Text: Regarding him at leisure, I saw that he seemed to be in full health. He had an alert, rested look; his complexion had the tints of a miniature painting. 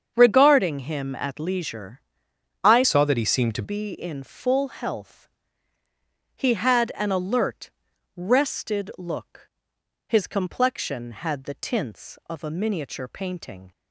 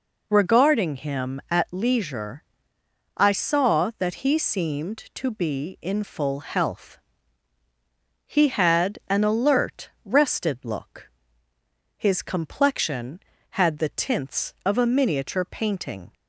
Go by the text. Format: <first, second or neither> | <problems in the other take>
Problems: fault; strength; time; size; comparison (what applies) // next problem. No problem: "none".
second | starts louder than the rest; strong; until 1.1 s; 7 dB // changes voice from "saw" to "to"; from 2.8 to 3.6 s; 0.8 s long